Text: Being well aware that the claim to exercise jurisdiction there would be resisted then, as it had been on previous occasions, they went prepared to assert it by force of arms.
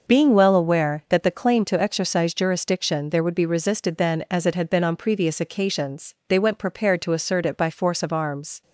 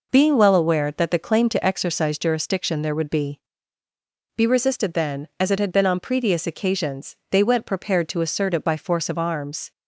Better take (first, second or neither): first